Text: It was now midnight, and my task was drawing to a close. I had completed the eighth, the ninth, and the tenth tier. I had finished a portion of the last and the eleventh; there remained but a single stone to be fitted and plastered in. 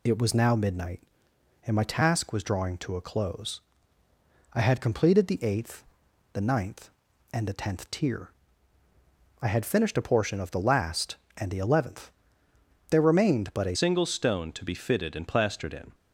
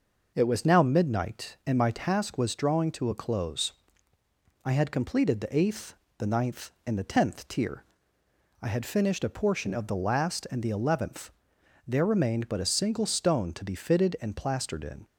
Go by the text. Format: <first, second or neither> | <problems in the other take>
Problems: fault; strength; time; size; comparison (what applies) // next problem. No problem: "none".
second | changes voice at "single"; from 13.7 s on; 2.2 s long